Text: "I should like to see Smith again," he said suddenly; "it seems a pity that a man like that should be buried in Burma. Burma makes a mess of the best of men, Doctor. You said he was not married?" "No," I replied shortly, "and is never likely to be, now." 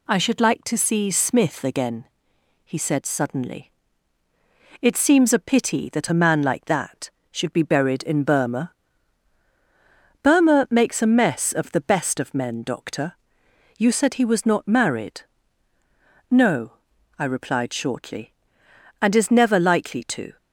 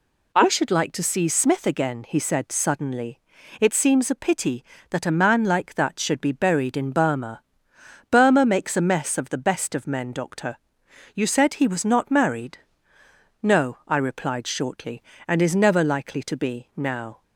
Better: second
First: stops before "be now"; at 20.3 s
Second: none

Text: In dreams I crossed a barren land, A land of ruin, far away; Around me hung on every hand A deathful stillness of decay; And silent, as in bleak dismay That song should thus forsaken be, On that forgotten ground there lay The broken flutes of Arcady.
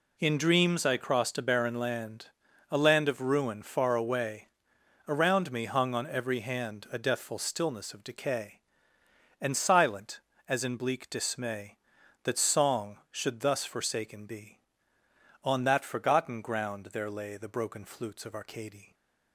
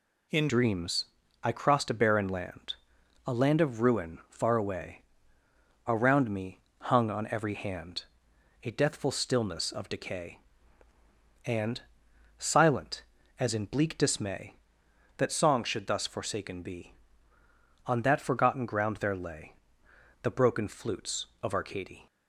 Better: first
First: none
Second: changes voice at "dreams"; from 0.4 s on; 21.6 s long // pauses between "dreams" and "I"; at 1.0 s; 0.38 s long // pauses between "me" and "hung"; slight; at 6.6 s; 0.18 s long // pauses between "hand" and "A"; noticeable; at 8.0 s; 0.58 s long // pauses between "And" and "silent"; noticeable; at 11.8 s; 0.56 s long // pauses between "lay" and "The"; noticeable; at 19.5 s; 0.70 s long

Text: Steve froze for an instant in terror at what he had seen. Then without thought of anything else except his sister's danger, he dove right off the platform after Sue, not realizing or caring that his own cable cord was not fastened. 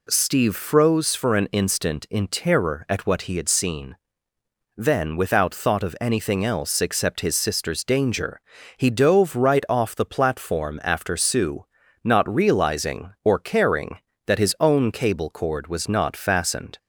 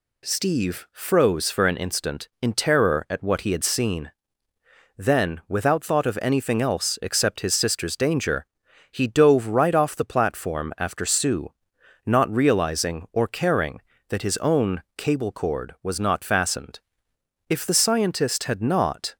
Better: first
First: none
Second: goes on to say "If the scientist had not"; from 17.4 s on; 1.6 s long

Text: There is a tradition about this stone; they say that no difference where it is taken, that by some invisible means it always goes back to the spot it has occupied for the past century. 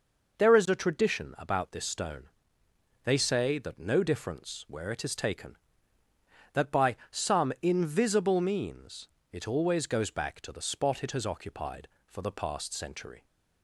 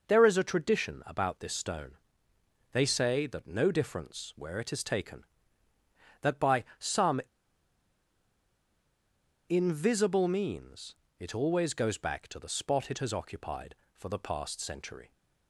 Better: first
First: pauses between "by" and "some"; slight; at 6.9 s; 0.16 s long // pauses between "means" and "it"; slight; at 9.0 s; 0.24 s long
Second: pauses between "by" and "some"; slight; at 6.6 s; 0.16 s long // pauses between "some" and "invisible"; strong; at 7.2 s; 2.2 s long // pauses between "means" and "it"; slight; at 10.9 s; 0.24 s long

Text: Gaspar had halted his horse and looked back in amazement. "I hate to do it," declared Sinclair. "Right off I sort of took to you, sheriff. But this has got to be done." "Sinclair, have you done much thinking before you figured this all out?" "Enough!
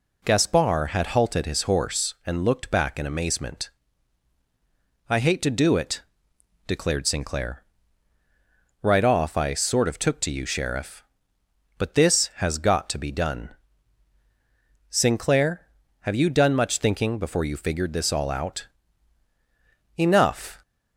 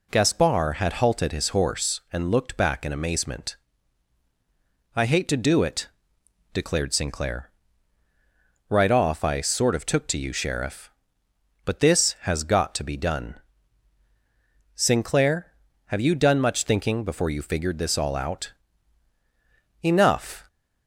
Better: neither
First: none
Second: none

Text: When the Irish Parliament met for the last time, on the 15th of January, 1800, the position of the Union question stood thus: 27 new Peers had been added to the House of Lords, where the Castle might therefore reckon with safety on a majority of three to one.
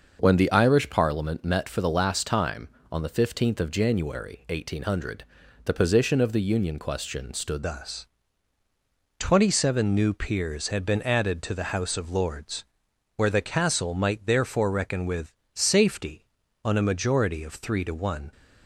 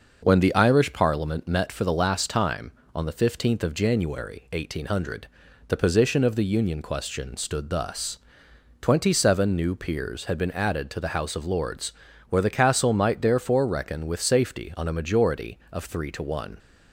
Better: second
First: starts louder than the rest; until 1.2 s; 6 dB // changes voice at "thus"; from 7.6 s on; 10.7 s long // pauses between "with" and "safety"; slight; at 15.3 s; 0.20 s long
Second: none

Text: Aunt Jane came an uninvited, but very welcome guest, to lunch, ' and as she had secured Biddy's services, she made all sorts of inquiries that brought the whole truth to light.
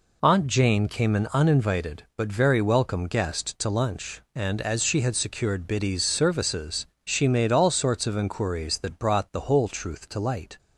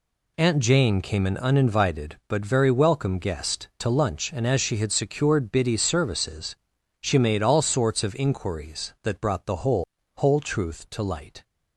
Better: first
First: none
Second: says "whole" twice; at 10.1 s

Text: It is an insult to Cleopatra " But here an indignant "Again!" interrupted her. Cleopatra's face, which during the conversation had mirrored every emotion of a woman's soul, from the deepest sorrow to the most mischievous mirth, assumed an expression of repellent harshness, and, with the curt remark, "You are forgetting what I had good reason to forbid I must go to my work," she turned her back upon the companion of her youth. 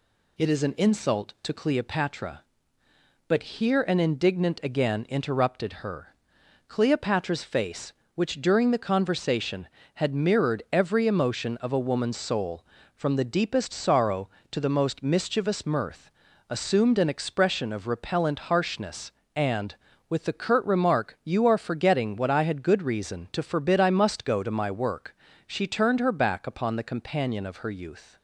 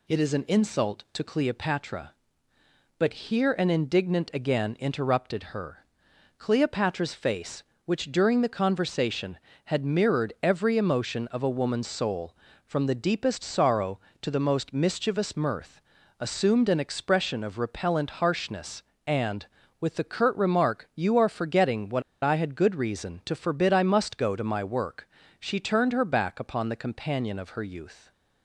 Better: first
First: none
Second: pauses between "what" and "I"; slight; at 22.0 s; 0.22 s long

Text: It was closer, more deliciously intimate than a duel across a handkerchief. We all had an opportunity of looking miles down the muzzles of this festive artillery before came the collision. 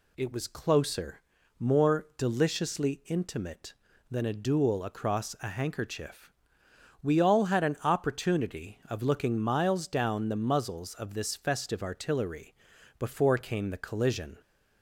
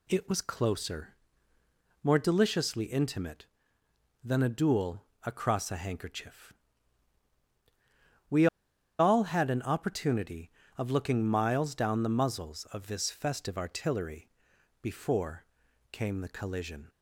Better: first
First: pauses between "artillery" and "before"; at 12.5 s; 0.44 s long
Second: pauses between "duel" and "across"; slight; at 5.0 s; 0.22 s long // pauses between "We" and "all"; noticeable; at 8.4 s; 0.52 s long // pauses between "artillery" and "before"; noticeable; at 14.2 s; 0.52 s long // pauses between "before" and "came"; noticeable; at 15.4 s; 0.46 s long

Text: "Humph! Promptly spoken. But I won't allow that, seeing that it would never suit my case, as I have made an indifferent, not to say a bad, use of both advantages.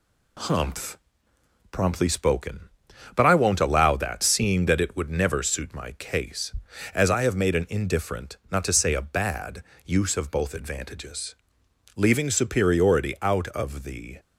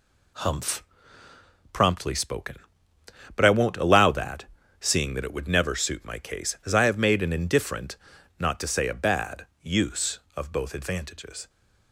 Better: second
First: goes on to say "Leaving superiority out of the"; strong; from 11.9 s on; 2.2 s long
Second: none

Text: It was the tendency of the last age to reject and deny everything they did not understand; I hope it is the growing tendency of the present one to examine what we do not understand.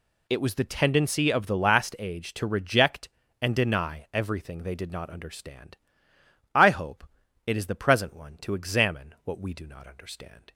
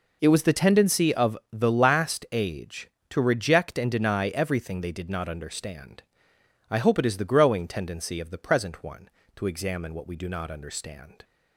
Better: second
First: pauses between "hope" and "it"; at 7.0 s; 0.38 s long // skips "growing tendency of the"; at 7.7 s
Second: none

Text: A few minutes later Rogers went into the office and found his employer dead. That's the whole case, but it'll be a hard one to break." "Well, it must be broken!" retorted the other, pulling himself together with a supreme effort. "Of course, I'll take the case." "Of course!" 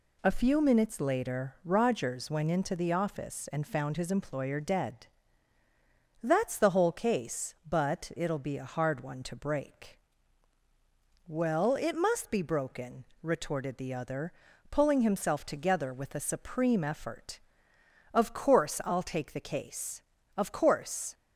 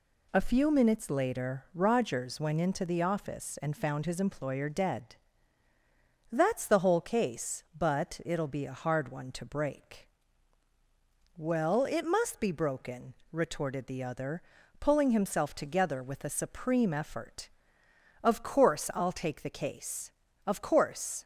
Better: neither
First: none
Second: none

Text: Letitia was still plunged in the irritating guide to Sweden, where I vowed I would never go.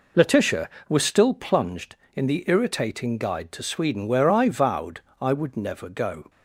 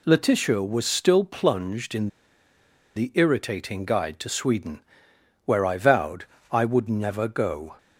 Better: first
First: pauses between "vowed" and "I"; slight; at 5.0 s; 0.18 s long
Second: pauses between "in" and "the"; noticeable; at 2.0 s; 0.88 s long // pauses between "vowed" and "I"; slight; at 6.2 s; 0.26 s long

